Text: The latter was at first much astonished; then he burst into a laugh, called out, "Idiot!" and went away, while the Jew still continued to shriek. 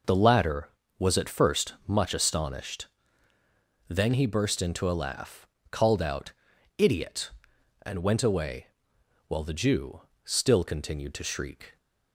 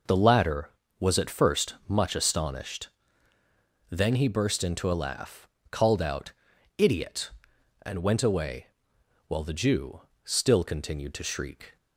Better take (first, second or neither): neither